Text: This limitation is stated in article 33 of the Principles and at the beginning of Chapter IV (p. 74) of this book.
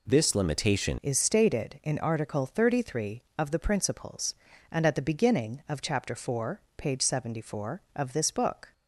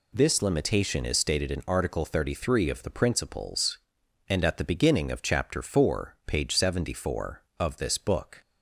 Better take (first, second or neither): second